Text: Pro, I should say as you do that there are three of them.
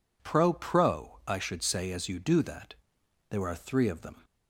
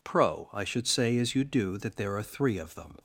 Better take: second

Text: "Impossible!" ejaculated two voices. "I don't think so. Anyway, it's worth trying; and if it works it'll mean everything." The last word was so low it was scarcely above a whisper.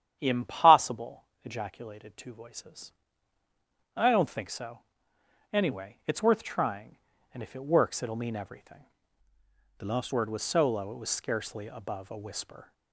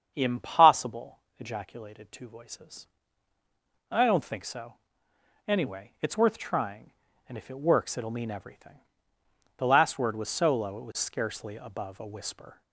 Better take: second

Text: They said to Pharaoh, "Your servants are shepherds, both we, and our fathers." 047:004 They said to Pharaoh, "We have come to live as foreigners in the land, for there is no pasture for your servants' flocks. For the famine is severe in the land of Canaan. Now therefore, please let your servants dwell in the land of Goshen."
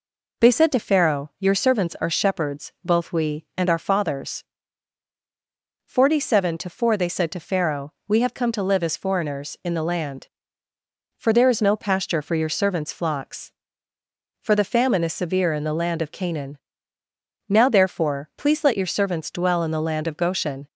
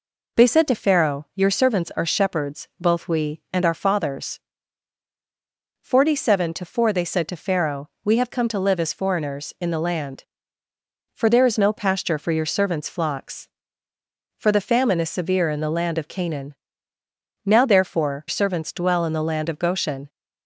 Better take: first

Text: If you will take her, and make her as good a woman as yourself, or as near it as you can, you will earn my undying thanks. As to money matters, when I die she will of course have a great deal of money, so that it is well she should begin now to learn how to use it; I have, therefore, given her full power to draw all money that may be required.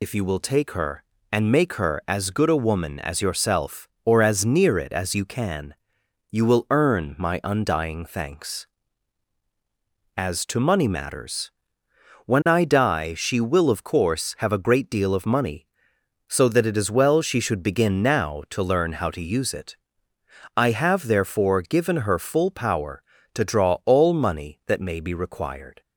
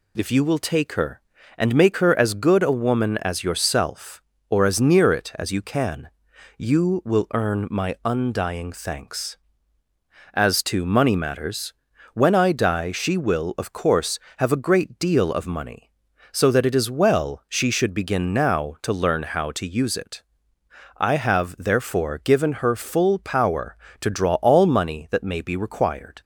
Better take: second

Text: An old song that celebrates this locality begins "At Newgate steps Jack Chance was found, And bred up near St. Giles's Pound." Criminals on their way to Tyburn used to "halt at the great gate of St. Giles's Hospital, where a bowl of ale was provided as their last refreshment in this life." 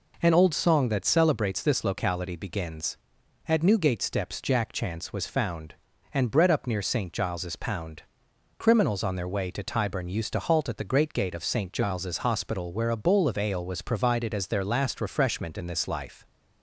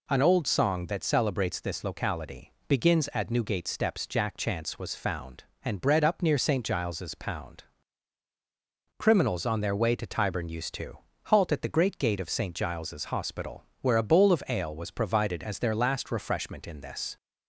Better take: first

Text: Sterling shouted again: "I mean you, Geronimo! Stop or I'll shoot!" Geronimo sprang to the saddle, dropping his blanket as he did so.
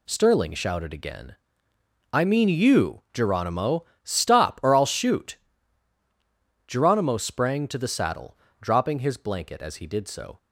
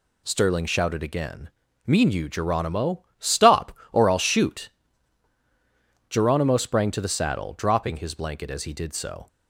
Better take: first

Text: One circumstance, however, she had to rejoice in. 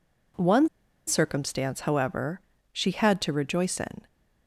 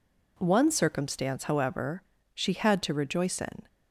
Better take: second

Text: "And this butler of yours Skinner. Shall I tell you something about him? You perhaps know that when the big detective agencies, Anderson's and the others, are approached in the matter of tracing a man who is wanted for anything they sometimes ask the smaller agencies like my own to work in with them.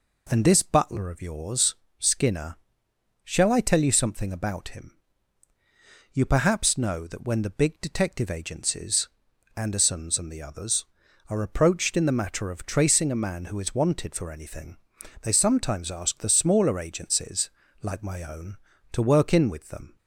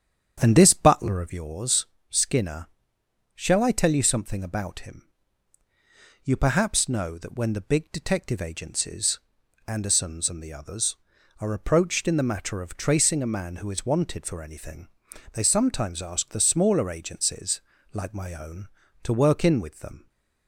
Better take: first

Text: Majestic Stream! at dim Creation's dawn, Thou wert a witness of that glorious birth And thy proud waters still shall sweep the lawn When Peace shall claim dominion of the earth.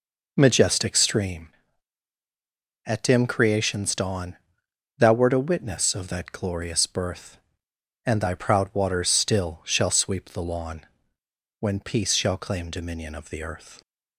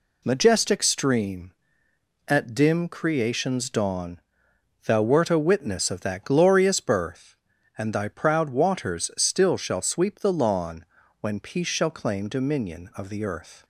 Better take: second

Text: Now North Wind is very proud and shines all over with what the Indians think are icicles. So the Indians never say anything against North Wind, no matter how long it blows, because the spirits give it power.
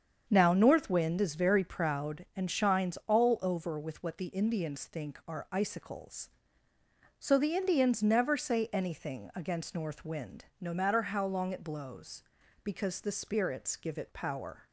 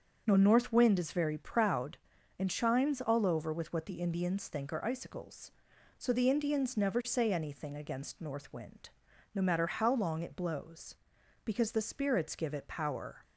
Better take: neither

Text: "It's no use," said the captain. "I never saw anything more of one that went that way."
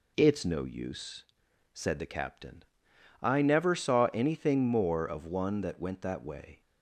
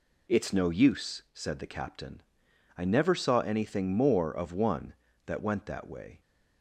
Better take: neither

